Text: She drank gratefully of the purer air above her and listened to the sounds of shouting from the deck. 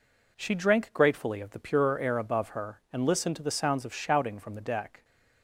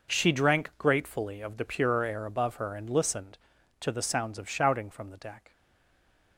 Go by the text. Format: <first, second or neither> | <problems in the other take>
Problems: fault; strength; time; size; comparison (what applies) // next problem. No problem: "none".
first | stays silent after the last word; slight; from 5.5 s on; 0.8 s long